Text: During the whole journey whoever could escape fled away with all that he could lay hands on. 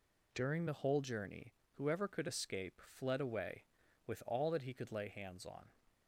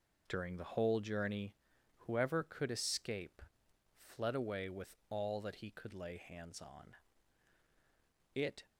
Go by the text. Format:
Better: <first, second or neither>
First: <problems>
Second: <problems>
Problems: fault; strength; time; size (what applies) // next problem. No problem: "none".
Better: first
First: pauses between "journey" and "whoever"; slight; at 1.5 s; 0.22 s long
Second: pauses between "journey" and "whoever"; noticeable; at 1.5 s; 0.46 s long // pauses between "escape" and "fled"; noticeable; at 3.4 s; 0.58 s long // goes on to say "It"; slight; from 8.3 s on; 0.30 s long